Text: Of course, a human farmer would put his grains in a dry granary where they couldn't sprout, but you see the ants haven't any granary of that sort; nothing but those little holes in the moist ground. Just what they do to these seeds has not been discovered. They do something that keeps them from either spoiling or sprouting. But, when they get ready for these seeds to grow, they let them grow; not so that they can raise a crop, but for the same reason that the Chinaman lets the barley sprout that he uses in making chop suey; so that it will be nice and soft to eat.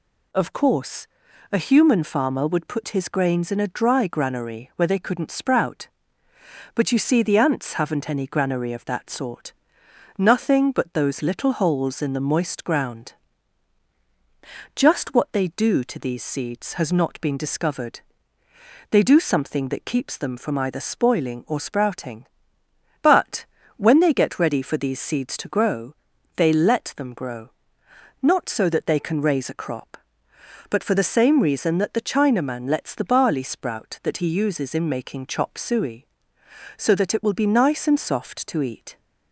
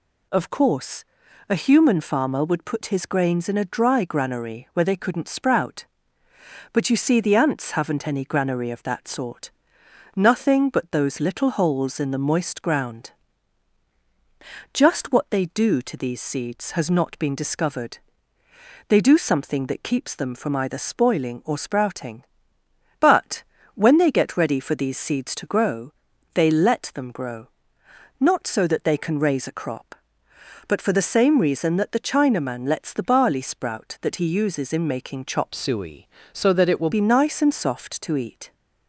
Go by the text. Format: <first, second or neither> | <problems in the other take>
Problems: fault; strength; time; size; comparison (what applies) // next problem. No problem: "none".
first | changes voice from "suey" to "will"; from 35.5 to 36.9 s; 1.4 s long